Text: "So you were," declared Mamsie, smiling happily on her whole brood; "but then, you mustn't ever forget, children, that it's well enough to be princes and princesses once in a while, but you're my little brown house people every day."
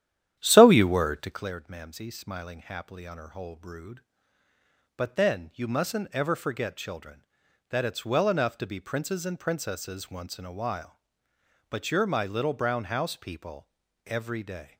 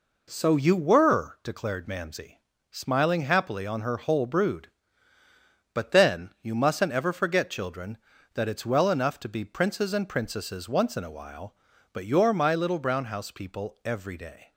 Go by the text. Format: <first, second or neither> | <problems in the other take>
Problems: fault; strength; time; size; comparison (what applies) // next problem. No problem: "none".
second | starts louder than the rest; strong; until 1.5 s; 11 dB // pauses between "people" and "every"; at 13.6 s; 0.38 s long